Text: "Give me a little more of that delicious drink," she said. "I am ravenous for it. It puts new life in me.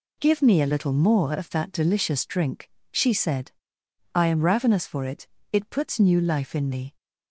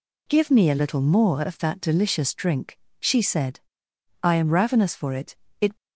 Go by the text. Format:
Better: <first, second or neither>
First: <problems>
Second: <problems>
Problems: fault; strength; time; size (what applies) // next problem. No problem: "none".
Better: first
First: none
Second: stops before "puts new life in me"; at 5.7 s